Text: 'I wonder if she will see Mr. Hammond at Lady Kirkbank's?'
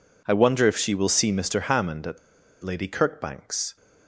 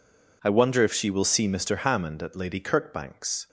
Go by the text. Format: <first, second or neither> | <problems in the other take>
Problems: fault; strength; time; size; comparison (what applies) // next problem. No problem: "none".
second | pauses between "at" and "Lady"; at 2.1 s; 0.45 s long